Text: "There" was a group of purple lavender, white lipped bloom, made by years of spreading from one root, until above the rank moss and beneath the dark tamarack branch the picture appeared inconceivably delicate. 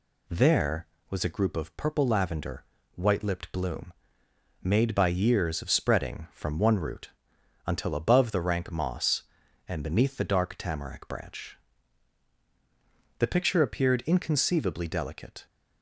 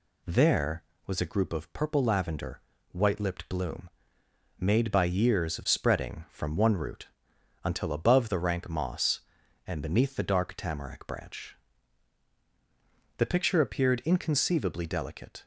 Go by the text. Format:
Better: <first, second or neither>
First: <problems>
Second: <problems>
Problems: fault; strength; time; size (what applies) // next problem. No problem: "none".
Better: neither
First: pauses between "branch" and "the"; strong; at 11.5 s; 1.6 s long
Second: pauses between "branch" and "the"; strong; at 11.5 s; 1.6 s long